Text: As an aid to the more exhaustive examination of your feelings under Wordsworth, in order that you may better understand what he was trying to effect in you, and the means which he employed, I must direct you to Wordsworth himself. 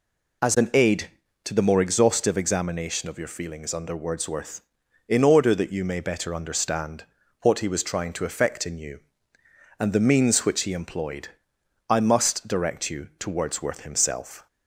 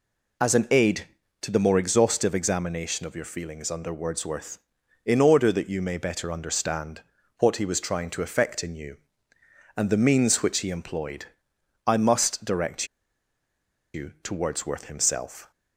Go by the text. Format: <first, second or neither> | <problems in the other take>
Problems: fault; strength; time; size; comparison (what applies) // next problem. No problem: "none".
first | pauses between "understand" and "what"; slight; at 7.0 s; 0.36 s long; slight in the first // pauses between "direct" and "you"; at 12.8 s; 1.0 s long